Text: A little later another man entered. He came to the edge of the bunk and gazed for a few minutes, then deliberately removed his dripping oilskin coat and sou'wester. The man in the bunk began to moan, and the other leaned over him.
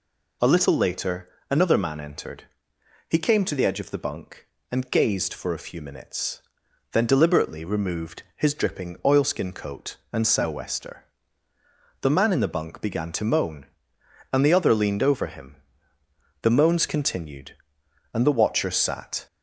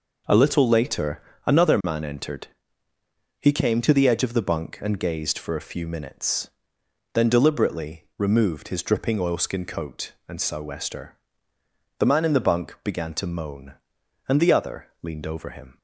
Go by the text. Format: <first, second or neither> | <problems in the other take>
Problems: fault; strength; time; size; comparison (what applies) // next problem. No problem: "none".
second | pauses between "later" and "another"; slight; at 1.2 s; 0.20 s long; slight in the second // goes on to say "The moans continued and the watcher sat"; strong; from 16.4 s on; 2.8 s long